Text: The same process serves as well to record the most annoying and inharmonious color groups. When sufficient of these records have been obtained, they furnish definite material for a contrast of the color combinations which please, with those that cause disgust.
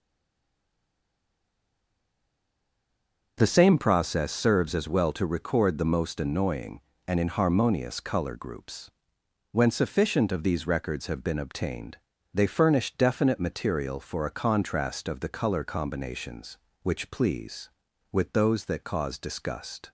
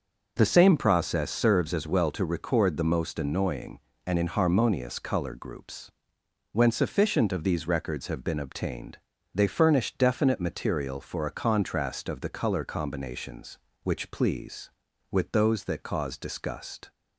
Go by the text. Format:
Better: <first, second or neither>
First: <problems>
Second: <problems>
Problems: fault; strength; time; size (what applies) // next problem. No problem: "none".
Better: second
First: stays silent before the first word; strong; until 3.3 s; 3.3 s long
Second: none